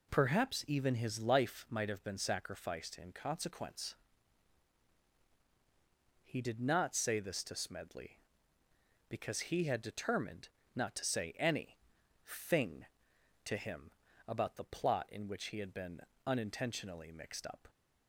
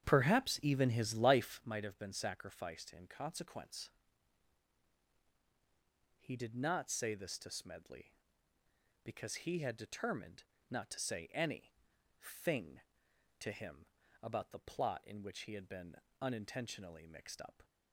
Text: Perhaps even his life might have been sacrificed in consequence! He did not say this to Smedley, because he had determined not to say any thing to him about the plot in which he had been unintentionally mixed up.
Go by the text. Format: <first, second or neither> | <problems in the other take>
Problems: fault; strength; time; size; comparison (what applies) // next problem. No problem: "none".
first | starts louder than the rest; strong; until 1.7 s; 9 dB // pauses between "determined" and "not"; slight; at 10.4 s; 0.26 s long; slight in the first // pauses between "any" and "thing"; noticeable; at 11.7 s; 0.52 s long; noticeable in the first // pauses between "him" and "about"; slight; at 13.8 s; 0.36 s long; slight in the first // pauses between "been" and "unintentionally"; slight; at 15.9 s; 0.26 s long; slight in the first